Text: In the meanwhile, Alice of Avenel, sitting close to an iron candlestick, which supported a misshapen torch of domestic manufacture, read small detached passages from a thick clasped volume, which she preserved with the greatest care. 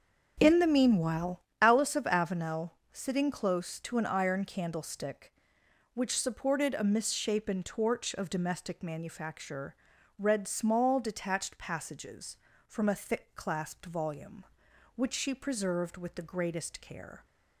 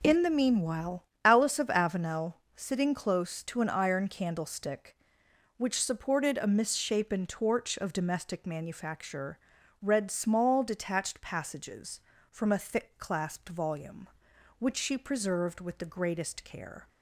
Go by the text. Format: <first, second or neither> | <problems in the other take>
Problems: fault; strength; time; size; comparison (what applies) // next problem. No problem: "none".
second | starts louder than the rest; until 1.6 s; 6.5 dB